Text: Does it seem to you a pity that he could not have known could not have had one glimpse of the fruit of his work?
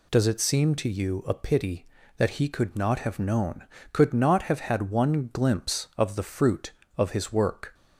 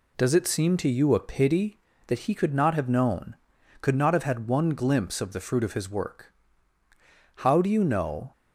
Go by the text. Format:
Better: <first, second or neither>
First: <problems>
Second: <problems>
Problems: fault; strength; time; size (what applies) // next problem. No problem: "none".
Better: first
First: none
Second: goes on to say "How do you know"; noticeable; from 7.3 s on; 0.94 s long